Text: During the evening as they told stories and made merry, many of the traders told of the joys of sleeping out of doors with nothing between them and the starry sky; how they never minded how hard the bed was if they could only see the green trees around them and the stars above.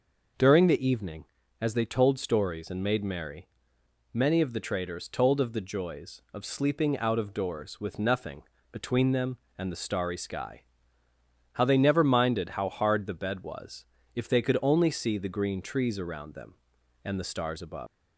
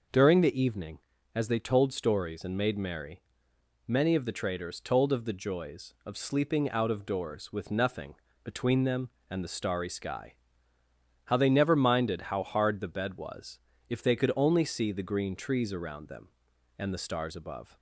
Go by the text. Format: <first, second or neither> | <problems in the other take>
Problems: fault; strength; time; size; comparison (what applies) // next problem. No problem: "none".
second | pauses between "nothing" and "between"; slight; at 8.4 s; 0.30 s long; slight in the second // pauses between "was" and "if"; slight; at 13.8 s; 0.30 s long; slight in the second // leaves "above" unfinished; at 17.8 s; 160 ms